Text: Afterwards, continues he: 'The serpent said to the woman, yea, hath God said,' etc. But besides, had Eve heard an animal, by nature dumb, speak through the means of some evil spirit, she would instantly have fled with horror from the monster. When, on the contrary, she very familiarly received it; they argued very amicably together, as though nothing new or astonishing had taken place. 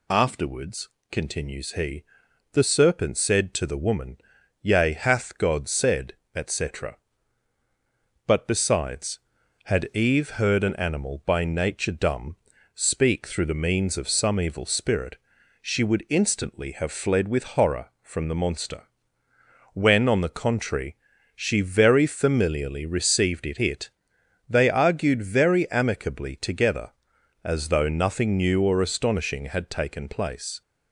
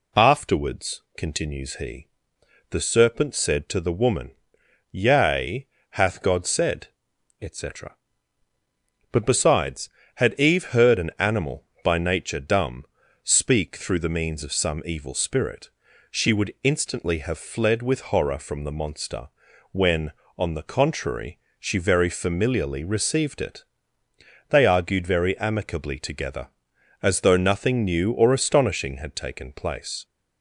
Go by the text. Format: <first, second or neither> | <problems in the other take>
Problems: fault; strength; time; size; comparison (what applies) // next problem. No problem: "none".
second | says "it" twice; at 23.5 s